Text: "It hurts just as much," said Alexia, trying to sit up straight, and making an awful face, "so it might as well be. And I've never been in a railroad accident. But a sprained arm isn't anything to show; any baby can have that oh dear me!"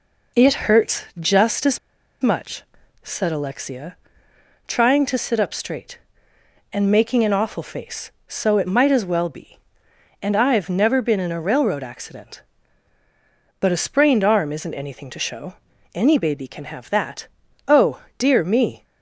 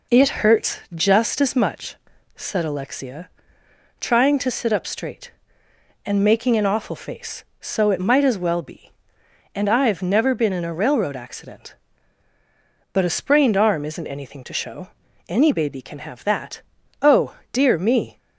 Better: second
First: pauses between "hurts" and "just"; slight; at 1.0 s; 0.16 s long // pauses between "as" and "much"; at 1.7 s; 0.42 s long // pauses between "that" and "oh"; at 17.2 s; 0.42 s long // pauses between "oh" and "dear"; slight; at 18.0 s; 0.16 s long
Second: pauses between "hurts" and "just"; slight; at 0.7 s; 0.16 s long // pauses between "that" and "oh"; at 16.6 s; 0.42 s long // pauses between "oh" and "dear"; slight; at 17.3 s; 0.16 s long

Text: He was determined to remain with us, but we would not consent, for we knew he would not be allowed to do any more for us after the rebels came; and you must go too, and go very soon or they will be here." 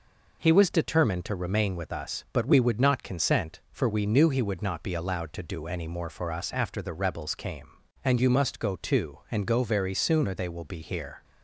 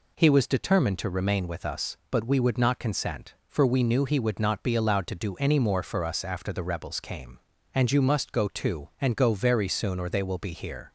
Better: neither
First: none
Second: none

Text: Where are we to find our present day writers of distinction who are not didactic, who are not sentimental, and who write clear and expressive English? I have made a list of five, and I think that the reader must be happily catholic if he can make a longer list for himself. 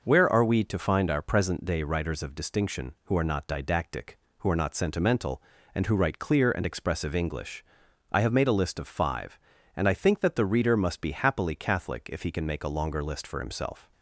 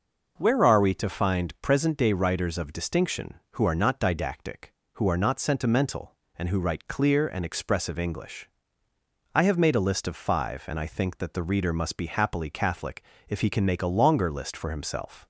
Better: first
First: none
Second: skips "our"; at 1.5 s // pauses between "catholic" and "if"; slight; at 13.0 s; 0.28 s long

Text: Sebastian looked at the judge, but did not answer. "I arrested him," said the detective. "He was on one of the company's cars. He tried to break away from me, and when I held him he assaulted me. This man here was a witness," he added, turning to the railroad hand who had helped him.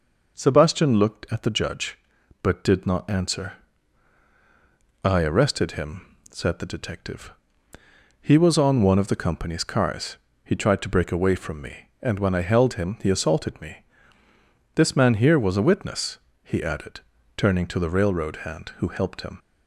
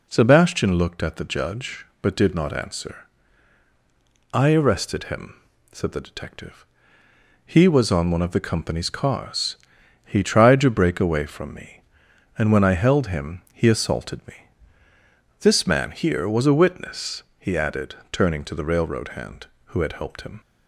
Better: second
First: skips "had"; at 18.8 s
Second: none

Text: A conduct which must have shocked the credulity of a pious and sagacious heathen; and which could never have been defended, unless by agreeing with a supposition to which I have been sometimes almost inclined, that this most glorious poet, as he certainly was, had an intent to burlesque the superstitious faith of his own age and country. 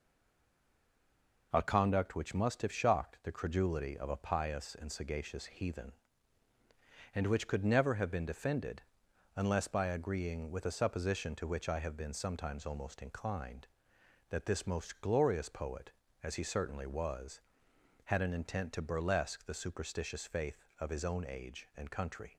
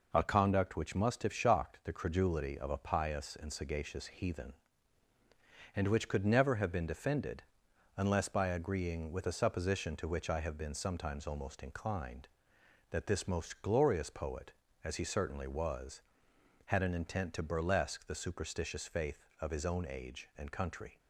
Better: second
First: stays silent before the first word; noticeable; until 1.5 s; 1.5 s long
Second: none

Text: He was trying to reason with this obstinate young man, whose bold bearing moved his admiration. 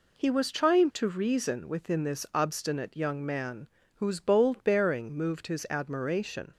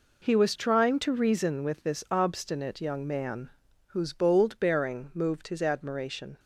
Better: second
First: says "within" for "with"; at 1.6 s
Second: none

